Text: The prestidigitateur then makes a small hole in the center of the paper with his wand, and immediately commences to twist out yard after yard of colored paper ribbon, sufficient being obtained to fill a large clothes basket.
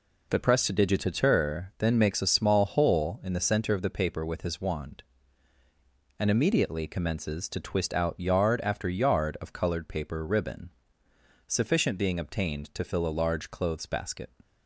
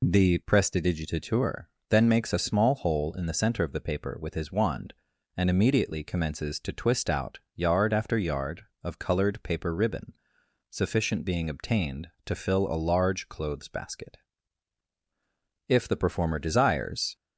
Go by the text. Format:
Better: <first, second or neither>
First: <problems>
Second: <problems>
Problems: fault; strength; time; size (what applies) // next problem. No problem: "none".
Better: first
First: none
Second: pauses between "prestidigitateur" and "then"; slight; at 1.6 s; 0.20 s long // pauses between "out" and "yard"; slight; at 7.3 s; 0.16 s long // goes on to say "If the performer desires"; from 15.6 s on; 1.4 s long